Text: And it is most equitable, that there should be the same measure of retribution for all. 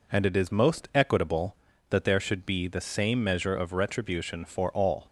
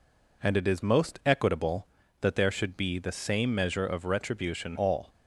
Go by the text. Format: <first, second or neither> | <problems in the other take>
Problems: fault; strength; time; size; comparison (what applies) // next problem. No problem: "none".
first | skips "for"; at 4.7 s